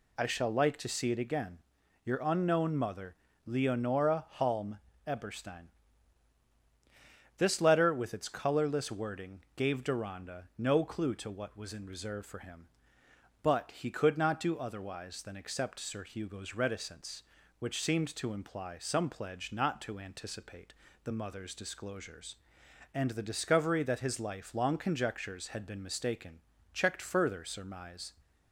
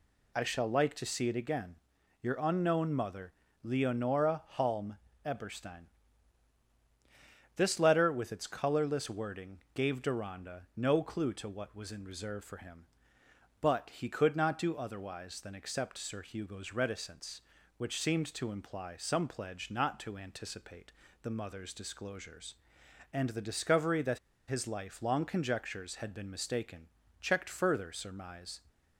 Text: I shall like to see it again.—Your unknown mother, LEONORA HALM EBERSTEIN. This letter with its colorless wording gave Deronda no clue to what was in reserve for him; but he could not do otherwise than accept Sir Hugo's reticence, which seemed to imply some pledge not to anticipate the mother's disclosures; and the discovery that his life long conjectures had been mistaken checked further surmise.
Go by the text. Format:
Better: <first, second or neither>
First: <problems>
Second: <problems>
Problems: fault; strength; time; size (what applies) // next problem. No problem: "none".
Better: first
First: pauses between "HALM" and "EBERSTEIN"; slight; at 4.7 s; 0.26 s long // pauses between "wording" and "gave"; slight; at 9.4 s; 0.16 s long // pauses between "anticipate" and "the"; slight; at 20.7 s; 0.30 s long // pauses between "mistaken" and "checked"; slight; at 26.3 s; 0.34 s long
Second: pauses between "LEONORA" and "HALM"; slight; at 4.4 s; 0.16 s long // pauses between "HALM" and "EBERSTEIN"; slight; at 4.9 s; 0.26 s long // pauses between "wording" and "gave"; slight; at 9.5 s; 0.16 s long // pauses between "anticipate" and "the"; slight; at 20.9 s; 0.30 s long // pauses between "that" and "his"; slight; at 24.1 s; 0.30 s long // pauses between "mistaken" and "checked"; slight; at 26.8 s; 0.34 s long